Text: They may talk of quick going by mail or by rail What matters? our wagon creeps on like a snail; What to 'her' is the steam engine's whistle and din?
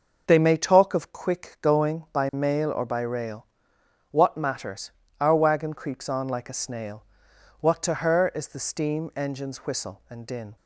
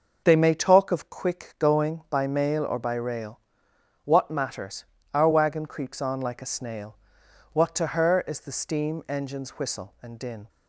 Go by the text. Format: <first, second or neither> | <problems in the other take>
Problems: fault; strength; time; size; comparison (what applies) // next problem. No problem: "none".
neither | pauses between "rail" and "What"; noticeable; the same in both